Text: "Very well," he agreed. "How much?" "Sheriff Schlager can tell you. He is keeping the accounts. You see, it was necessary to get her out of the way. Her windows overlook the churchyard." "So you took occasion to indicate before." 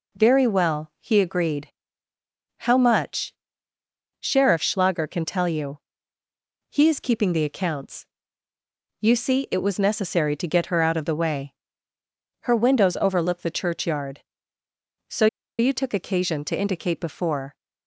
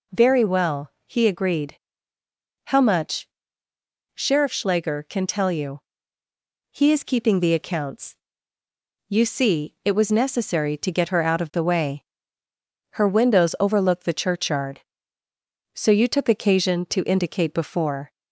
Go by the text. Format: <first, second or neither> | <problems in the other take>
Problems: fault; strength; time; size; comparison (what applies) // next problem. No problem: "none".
second | pauses between "So" and "you"; slight; at 15.2 s; 0.32 s long